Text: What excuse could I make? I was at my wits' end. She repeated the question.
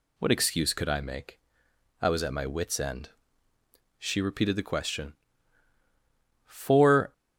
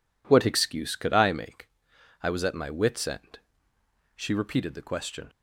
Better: second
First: goes on to say "For"; noticeable; from 6.4 s on; 0.66 s long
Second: none

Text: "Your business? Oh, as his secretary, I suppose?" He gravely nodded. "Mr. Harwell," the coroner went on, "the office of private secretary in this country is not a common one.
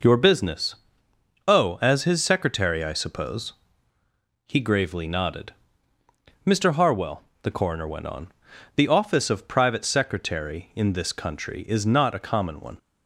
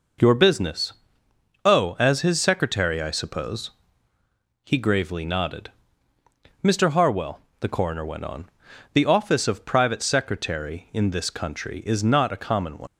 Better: first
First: none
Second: leaves "one" unfinished; at 12.8 s; 80 ms

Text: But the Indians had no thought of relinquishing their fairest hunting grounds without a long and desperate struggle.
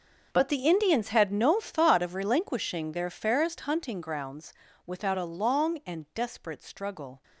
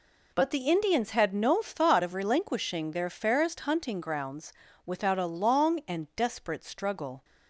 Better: second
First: gets quieter; strong; throughout; 15.5 dB // pauses between "grounds" and "without"; slight; at 4.5 s; 0.34 s long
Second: pauses between "grounds" and "without"; slight; at 4.5 s; 0.34 s long

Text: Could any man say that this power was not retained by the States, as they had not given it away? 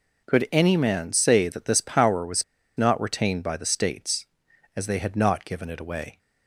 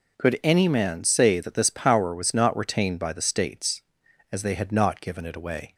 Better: second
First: pauses between "was" and "not"; slight; at 2.4 s; 0.34 s long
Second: none

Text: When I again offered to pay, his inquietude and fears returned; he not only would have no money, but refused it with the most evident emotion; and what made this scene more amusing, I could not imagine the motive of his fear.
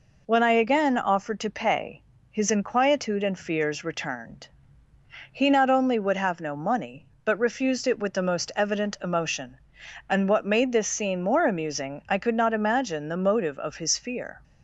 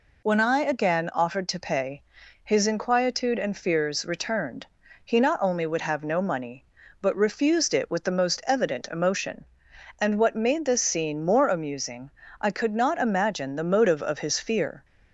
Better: neither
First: none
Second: none

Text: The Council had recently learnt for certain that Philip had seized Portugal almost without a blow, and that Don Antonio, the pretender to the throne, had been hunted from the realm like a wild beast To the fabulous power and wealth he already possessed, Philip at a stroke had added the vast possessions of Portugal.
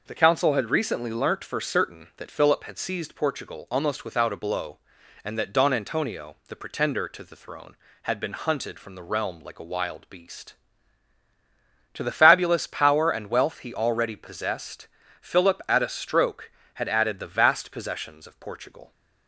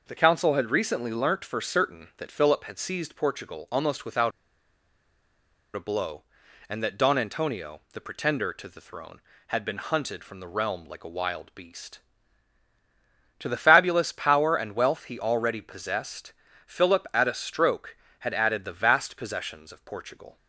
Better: first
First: none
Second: pauses between "without" and "a"; strong; at 4.3 s; 1.4 s long

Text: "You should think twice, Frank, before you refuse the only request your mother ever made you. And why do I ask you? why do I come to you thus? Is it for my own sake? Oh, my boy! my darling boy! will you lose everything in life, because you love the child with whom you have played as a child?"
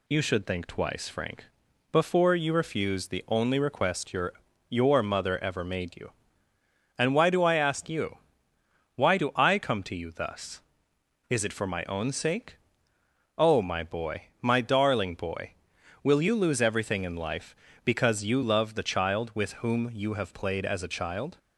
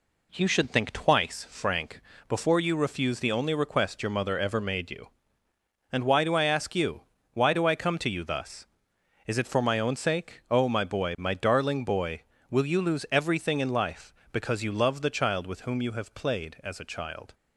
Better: second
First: says "your" twice; at 4.6 s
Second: none

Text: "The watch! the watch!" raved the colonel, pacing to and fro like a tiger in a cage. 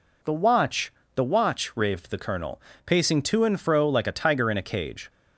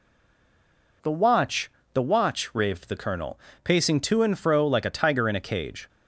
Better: first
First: none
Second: stays silent before the first word; until 1.0 s; 1.0 s long

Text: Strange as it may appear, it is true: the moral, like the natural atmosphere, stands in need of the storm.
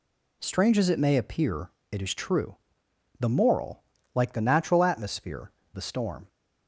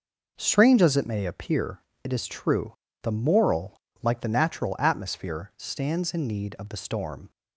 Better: second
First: skips "stands in need of"; at 5.6 s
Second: none

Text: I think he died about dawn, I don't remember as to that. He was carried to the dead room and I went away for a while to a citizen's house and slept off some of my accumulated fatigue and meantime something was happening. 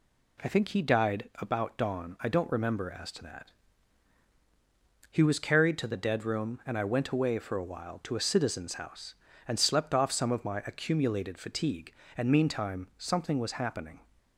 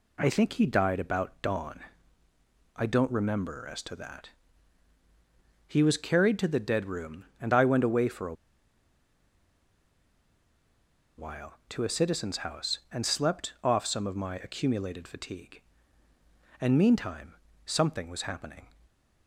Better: first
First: none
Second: pauses between "a" and "while"; strong; at 8.3 s; 2.8 s long // pauses between "meantime" and "something"; slight; at 17.3 s; 0.32 s long

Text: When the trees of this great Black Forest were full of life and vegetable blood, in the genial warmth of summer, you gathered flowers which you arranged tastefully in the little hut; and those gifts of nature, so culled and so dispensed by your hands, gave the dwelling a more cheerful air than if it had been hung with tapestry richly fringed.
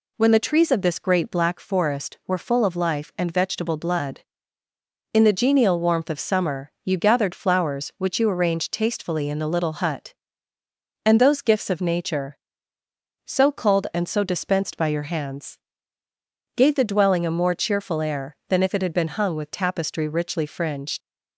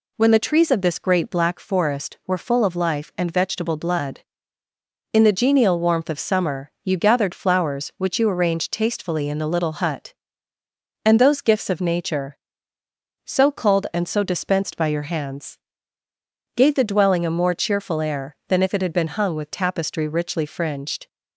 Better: second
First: leaves "fringed" unfinished; at 21.0 s; 70 ms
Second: none

